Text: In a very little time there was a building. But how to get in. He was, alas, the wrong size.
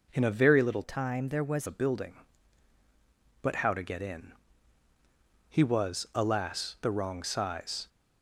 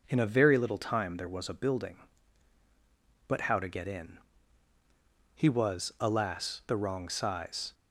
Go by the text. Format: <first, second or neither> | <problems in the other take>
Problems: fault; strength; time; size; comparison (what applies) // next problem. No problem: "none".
second | changes voice from "time" to "was"; from 0.8 to 1.6 s; 0.8 s long